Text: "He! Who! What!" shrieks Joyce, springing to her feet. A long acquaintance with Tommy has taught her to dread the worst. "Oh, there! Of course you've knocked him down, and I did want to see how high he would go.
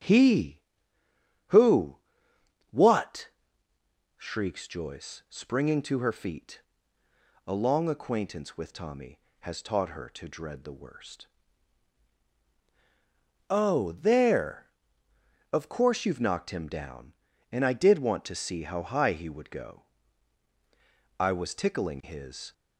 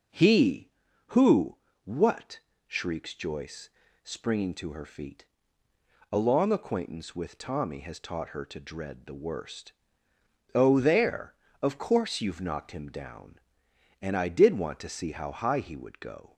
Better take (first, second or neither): second